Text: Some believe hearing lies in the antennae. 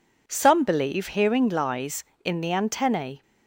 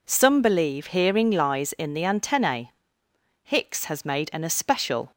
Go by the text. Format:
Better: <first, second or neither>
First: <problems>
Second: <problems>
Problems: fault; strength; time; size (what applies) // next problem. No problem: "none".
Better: first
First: none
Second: goes on to say "Hicks has made an especial"; strong; from 3.4 s on; 1.6 s long